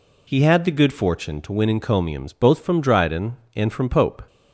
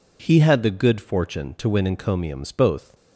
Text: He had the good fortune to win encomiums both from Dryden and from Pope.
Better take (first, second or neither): first